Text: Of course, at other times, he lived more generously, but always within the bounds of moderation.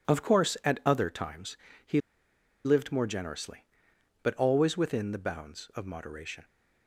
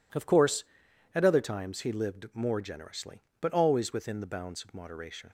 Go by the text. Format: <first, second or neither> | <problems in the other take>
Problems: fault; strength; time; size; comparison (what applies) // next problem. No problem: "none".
second | pauses between "he" and "lived"; noticeable; at 1.9 s; 0.66 s long